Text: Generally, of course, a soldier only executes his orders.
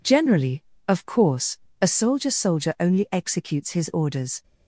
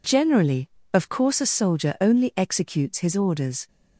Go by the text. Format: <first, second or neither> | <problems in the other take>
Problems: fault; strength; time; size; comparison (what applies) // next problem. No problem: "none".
second | says "soldier" twice; at 2.3 s